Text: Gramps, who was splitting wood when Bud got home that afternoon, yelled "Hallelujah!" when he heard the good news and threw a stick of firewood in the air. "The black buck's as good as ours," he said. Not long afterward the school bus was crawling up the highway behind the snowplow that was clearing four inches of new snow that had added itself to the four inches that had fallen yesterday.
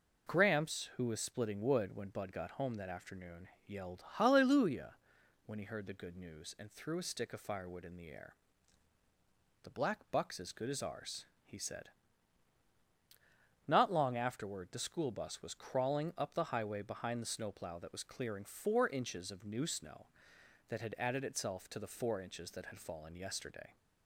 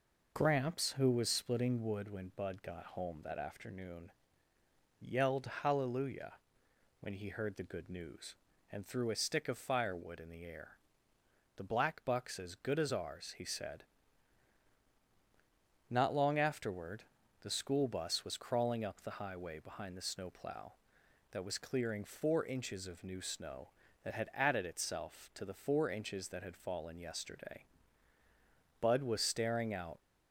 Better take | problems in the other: first | pauses between "yelled" and "Hallelujah"; slight; at 5.4 s; 0.16 s long // pauses between "afterward" and "the"; slight; at 17.0 s; 0.36 s long // goes on to say "Bud was staring out"; noticeable; from 28.8 s on; 1.1 s long

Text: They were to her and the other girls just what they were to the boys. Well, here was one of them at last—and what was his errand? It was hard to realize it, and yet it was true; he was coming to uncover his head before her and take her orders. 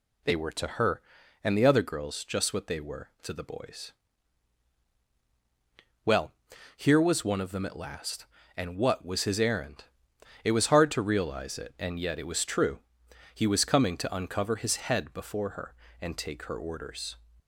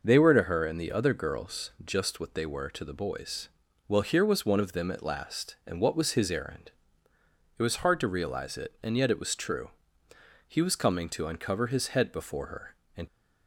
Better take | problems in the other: first | stops before "take her orders"; at 13.0 s

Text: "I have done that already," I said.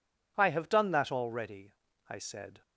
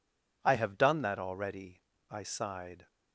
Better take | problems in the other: first | says "sighed" for "said"; at 2.2 s

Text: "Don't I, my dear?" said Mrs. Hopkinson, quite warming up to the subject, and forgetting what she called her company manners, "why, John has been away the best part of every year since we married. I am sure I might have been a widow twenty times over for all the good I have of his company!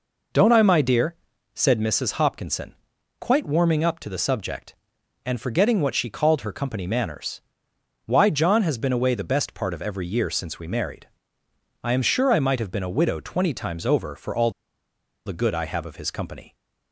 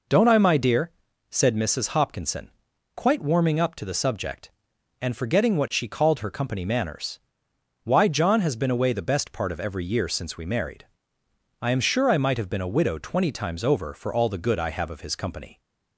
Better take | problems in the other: second | pauses between "all" and "the"; noticeable; at 14.5 s; 0.74 s long

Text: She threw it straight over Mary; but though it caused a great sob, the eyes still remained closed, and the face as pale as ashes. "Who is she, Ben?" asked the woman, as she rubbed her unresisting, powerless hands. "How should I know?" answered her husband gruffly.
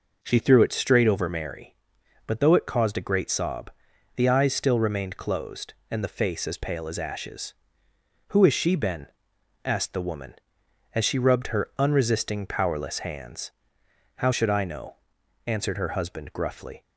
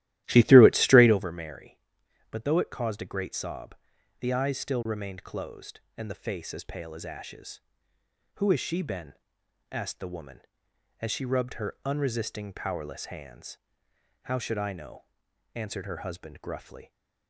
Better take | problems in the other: first | starts louder than the rest; strong; until 1.2 s; 14.5 dB

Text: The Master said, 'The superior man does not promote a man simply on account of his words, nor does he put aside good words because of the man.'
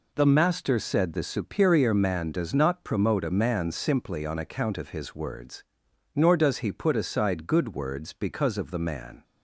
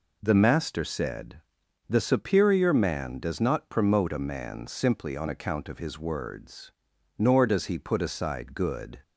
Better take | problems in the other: first | stops before "words because of the man"; at 9.0 s

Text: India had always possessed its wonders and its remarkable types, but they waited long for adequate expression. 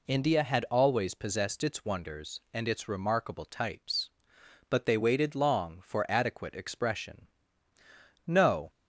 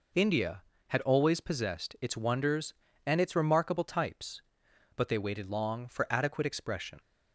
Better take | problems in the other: second | goes on to say "No"; slight; from 8.2 s on; 0.44 s long

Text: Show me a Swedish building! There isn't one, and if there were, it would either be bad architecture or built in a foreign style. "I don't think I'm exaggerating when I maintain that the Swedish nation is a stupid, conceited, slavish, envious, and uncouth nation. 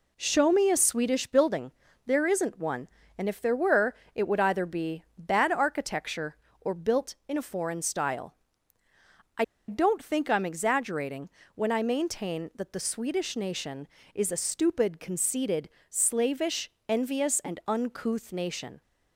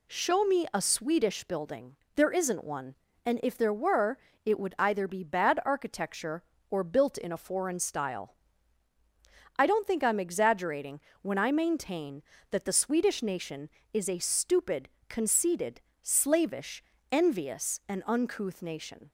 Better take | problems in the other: second | pauses between "be" and "bad"; slight; at 5.0 s; 0.16 s long // pauses between "I" and "don't"; slight; at 9.4 s; 0.24 s long // pauses between "exaggerating" and "when"; slight; at 11.2 s; 0.26 s long; slight in the second

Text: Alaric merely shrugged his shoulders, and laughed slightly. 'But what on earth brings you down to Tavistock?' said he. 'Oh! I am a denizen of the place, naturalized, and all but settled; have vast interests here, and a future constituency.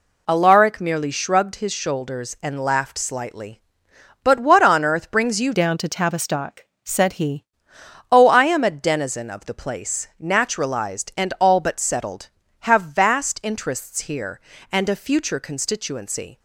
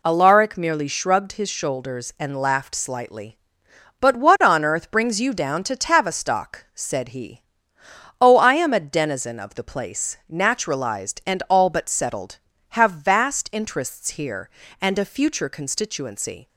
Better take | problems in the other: second | changes voice from "down" to "he"; from 5.5 to 7.4 s; 1.9 s long

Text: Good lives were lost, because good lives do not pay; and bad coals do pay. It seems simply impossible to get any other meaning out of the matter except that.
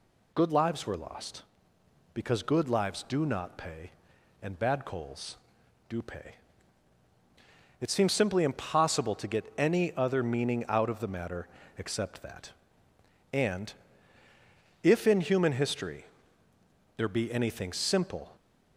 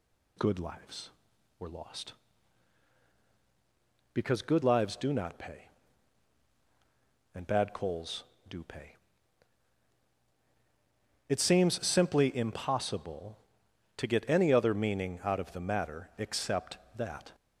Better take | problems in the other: second | pauses between "matter" and "except"; slight; at 11.4 s; 0.32 s long // goes on to say "And if in human history there be anything simple"; strong; from 13.3 s on; 5.0 s long

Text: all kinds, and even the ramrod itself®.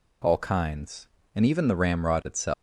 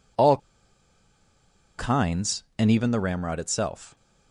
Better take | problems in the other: first | pauses between "all" and "kinds"; strong; at 0.3 s; 1.4 s long

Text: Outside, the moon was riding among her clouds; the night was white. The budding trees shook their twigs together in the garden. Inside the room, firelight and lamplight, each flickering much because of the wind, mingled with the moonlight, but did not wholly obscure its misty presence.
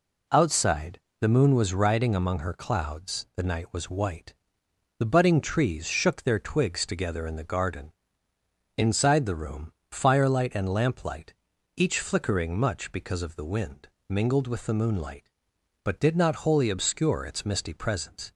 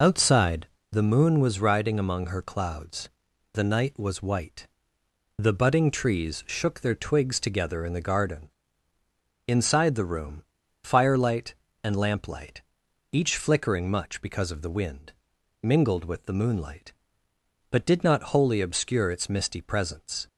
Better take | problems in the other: first | loses the start of "Outside"; at 0.0 s; 30 ms

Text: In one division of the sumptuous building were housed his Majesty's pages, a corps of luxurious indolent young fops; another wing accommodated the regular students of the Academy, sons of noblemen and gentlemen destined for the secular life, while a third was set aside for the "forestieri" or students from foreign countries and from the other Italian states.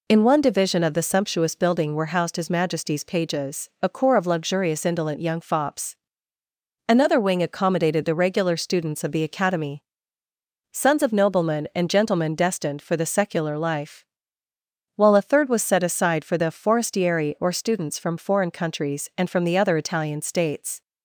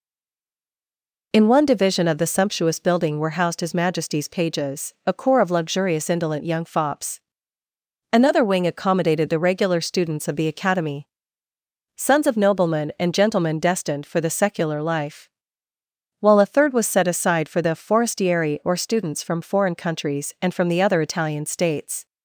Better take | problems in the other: first | stays silent before the first word; noticeable; until 1.3 s; 1.3 s long

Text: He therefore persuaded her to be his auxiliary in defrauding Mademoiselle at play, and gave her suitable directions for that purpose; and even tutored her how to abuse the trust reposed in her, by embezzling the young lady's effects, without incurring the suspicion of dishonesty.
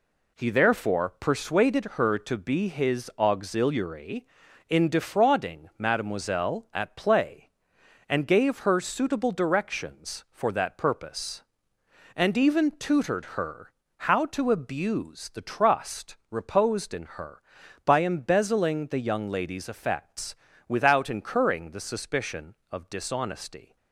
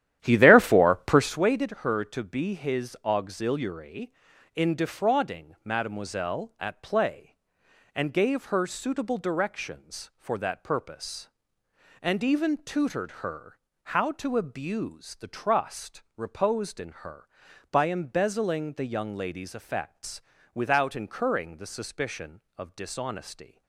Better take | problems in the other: first | starts louder than the rest; strong; until 1.5 s; 11.5 dB // pauses between "her" and "how"; slight; at 13.5 s; 0.26 s long; slight in the first // pauses between "trust" and "reposed"; slight; at 16.0 s; 0.16 s long; slight in the first

